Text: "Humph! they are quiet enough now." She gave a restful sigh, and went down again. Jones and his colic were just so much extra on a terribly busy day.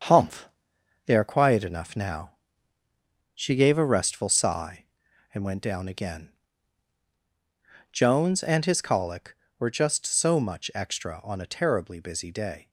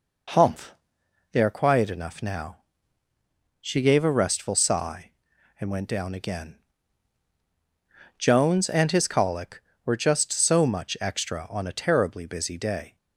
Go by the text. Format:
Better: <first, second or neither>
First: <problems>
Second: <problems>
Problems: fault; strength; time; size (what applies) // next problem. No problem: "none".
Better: second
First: gets quieter; throughout; 6.5 dB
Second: none